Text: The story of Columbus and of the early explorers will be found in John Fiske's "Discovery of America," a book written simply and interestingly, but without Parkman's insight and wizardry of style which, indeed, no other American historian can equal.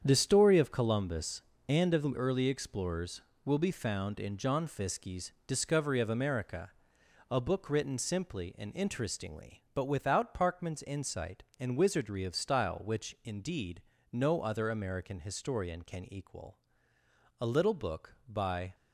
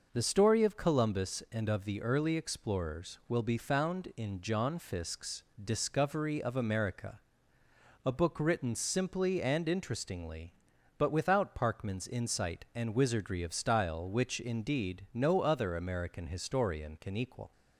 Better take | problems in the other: second | starts louder than the rest; strong; until 1.0 s; 8 dB // pauses between "Fiske's" and "Discovery"; slight; at 5.3 s; 0.16 s long; slight in the second // goes on to say "A little book by"; from 17.3 s on; 1.3 s long

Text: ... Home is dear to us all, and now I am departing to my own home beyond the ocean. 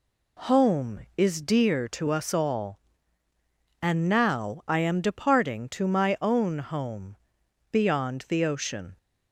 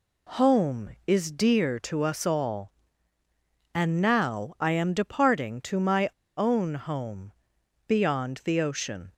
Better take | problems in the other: first | pauses between "my" and "own"; slight; at 6.0 s; 0.27 s long // pauses between "home" and "beyond"; noticeable; at 7.3 s; 0.56 s long; noticeable in the first

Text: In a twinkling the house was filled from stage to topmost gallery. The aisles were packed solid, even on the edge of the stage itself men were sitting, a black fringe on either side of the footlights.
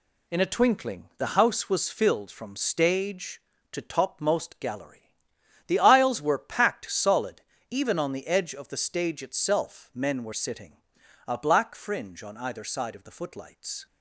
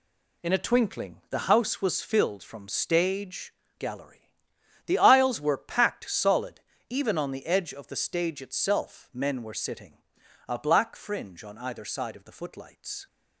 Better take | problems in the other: first | skips "to topmost"; at 3.6 s

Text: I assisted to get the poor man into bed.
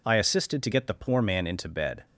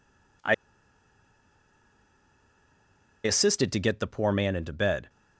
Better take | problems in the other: first | pauses between "I" and "assisted"; strong; at 0.5 s; 2.7 s long

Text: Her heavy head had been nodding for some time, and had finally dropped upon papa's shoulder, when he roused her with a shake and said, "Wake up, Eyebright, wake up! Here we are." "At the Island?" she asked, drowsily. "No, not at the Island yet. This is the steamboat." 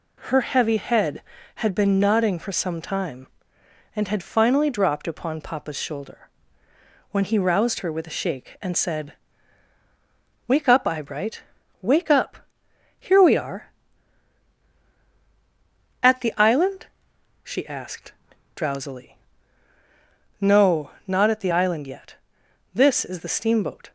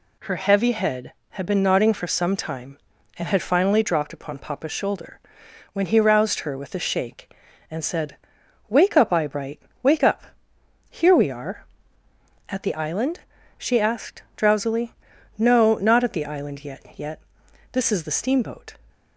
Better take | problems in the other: first | says "yet" twice; at 16.9 s

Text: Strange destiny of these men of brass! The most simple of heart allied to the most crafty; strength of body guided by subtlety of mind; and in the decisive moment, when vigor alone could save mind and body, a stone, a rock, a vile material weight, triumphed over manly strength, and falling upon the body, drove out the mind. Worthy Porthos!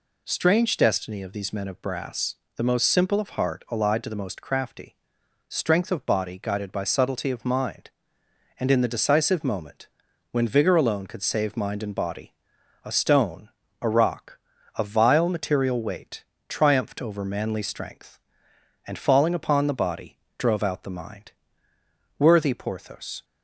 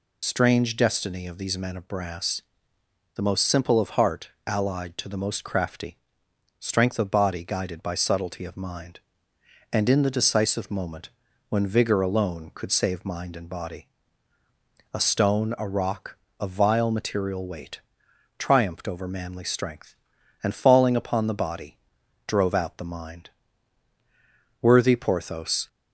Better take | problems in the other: first | loses the start of "Strange"; at 0.2 s; 50 ms // pauses between "heart" and "allied"; slight; at 4.2 s; 0.18 s long

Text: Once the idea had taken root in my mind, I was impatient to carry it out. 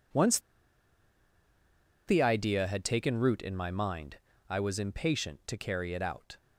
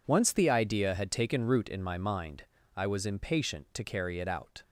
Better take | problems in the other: second | pauses between "Once" and "the"; strong; at 0.3 s; 1.6 s long

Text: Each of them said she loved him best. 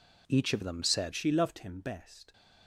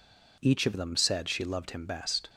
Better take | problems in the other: second | changes voice at "she"; from 1.1 s on; 1.2 s long

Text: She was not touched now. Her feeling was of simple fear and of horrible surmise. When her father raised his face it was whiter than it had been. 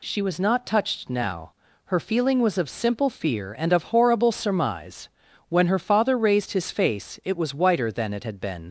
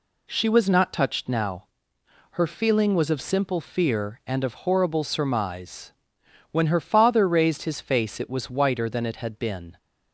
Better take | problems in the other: second | leaves "been" unfinished; at 8.6 s; 60 ms

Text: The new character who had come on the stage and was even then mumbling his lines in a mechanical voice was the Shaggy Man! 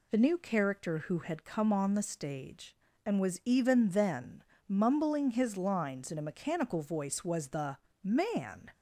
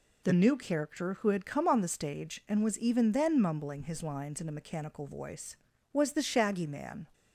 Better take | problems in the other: second | pauses between "then" and "mumbling"; slight; at 4.4 s; 0.24 s long // skips "Shaggy"; at 7.9 s

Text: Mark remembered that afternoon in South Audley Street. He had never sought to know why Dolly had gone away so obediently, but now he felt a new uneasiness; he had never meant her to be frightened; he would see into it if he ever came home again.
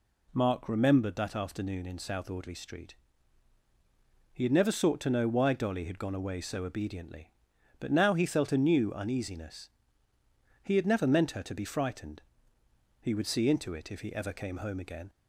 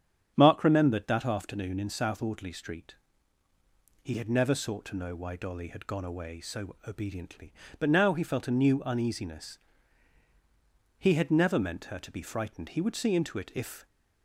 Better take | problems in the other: first | starts louder than the rest; strong; until 1.3 s; 8.5 dB // stops before "he ever came home again"; at 13.8 s

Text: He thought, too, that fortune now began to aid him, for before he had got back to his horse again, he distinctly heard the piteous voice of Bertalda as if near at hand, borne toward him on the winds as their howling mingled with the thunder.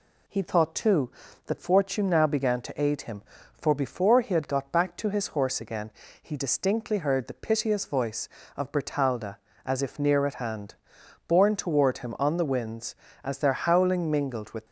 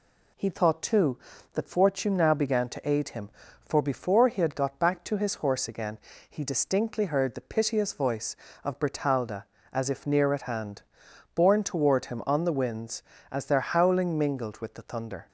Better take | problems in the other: second | stops before "the thunder"; at 14.6 s

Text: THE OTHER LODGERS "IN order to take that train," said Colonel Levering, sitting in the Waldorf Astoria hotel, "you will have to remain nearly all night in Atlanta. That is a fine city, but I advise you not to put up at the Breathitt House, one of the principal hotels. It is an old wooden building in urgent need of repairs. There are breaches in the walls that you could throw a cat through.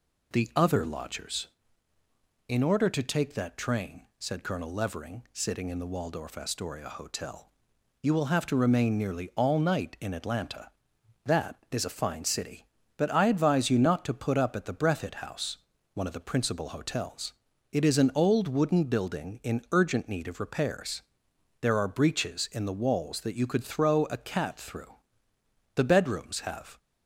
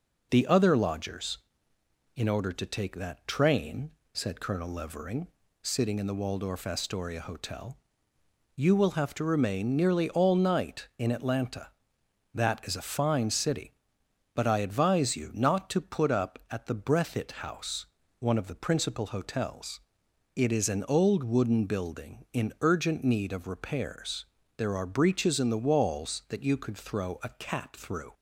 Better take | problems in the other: second | goes on to say "The bedrooms have"; noticeable; from 25.7 s on; 1.0 s long

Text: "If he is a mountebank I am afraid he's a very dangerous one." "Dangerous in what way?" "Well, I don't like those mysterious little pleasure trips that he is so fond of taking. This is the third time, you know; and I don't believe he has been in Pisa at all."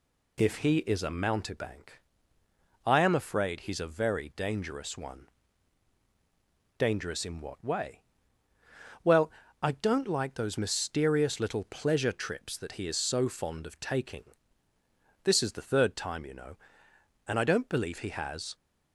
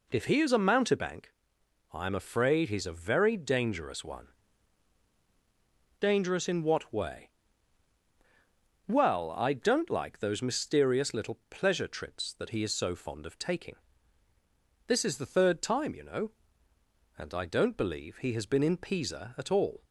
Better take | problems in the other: second | pauses between "mountebank" and "I"; noticeable; at 2.0 s; 0.86 s long; noticeable in the second // stops before "been in Pisa at all"; at 18.5 s

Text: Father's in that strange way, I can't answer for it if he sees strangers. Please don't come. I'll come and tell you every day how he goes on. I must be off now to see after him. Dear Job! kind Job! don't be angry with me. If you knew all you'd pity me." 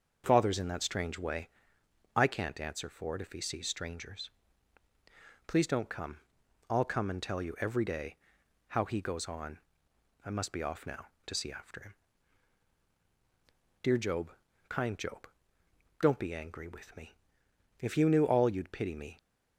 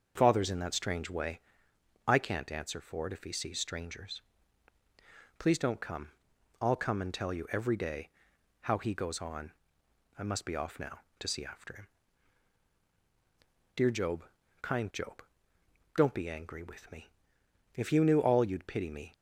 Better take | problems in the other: neither | starts louder than the rest; the same in both // pauses between "day" and "how"; noticeable; the same in both

